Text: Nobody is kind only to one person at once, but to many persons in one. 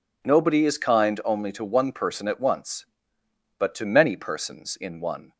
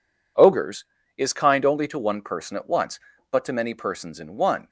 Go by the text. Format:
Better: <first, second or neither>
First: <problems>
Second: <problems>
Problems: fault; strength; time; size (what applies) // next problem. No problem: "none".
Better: first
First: none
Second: says "Ogres" for "Nobody"; at 0.3 s